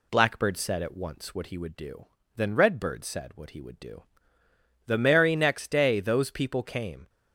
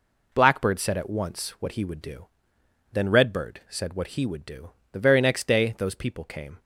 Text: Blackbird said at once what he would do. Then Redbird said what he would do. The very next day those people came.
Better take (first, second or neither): second